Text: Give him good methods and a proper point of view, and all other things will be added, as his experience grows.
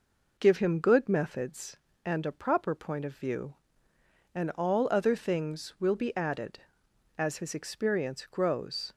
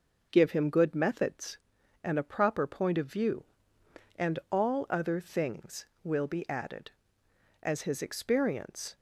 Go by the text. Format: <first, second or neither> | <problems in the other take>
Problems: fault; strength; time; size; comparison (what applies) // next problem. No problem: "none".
first | starts louder than the rest; noticeable; until 1.3 s; 6 dB // stops before "grows"; at 8.9 s